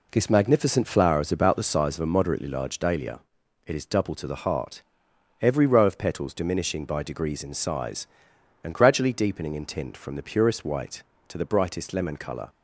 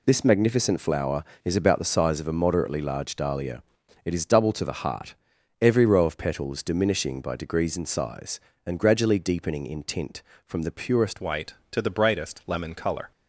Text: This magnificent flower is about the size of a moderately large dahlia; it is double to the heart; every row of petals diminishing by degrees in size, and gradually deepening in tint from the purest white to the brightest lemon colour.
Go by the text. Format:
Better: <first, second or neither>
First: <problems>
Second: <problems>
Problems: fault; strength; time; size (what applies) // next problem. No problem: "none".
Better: first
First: none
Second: changes voice at "white"; from 11.2 s on; 1.9 s long